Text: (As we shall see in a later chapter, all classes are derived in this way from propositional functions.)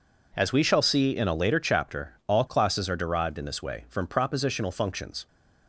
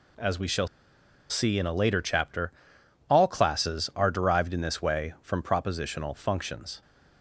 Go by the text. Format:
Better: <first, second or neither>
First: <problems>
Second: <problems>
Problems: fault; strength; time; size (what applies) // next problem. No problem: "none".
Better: first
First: none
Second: pauses between "shall" and "see"; noticeable; at 0.6 s; 0.62 s long